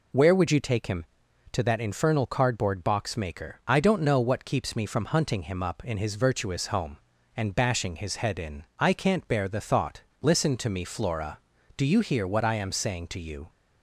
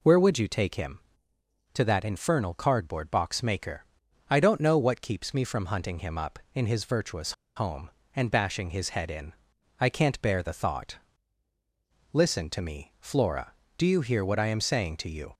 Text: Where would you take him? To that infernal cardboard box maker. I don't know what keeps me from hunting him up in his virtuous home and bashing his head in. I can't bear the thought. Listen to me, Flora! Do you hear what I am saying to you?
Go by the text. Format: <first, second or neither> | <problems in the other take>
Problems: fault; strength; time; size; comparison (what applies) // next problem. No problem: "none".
first | pauses between "virtuous" and "home"; slight; at 7.3 s; 0.24 s long